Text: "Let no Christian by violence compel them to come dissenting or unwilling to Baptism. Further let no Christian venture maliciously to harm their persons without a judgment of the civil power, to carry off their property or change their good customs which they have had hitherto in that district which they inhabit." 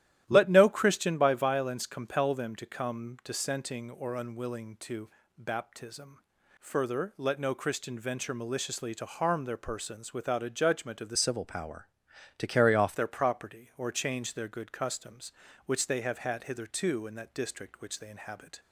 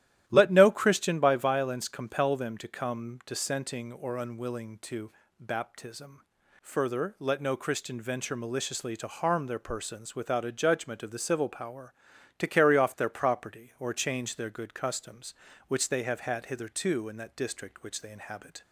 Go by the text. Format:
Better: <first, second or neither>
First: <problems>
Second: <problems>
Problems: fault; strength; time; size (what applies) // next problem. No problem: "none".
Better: second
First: starts louder than the rest; strong; until 1.2 s; 13 dB // pauses between "to" and "Baptism"; slight; at 5.1 s; 0.26 s long // changes voice from "civil" to "off"; from 11.1 to 12.9 s; 1.8 s long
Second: starts louder than the rest; strong; until 1.2 s; 13 dB // pauses between "to" and "Baptism"; slight; at 5.1 s; 0.26 s long